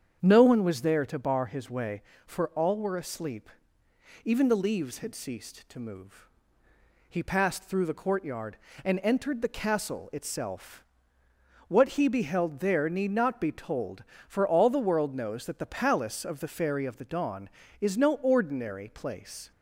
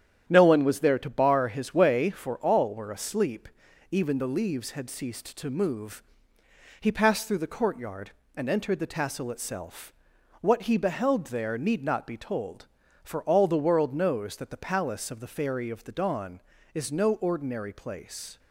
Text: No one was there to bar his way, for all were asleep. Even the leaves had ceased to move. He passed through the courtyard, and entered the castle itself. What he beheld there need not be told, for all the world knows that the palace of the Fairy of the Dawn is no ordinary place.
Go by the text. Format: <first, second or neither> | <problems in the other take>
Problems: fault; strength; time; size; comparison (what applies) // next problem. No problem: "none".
first | starts louder than the rest; strong; until 1.2 s; 9.5 dB; strong in the first // says "tassel" for "castle"; at 8.8 s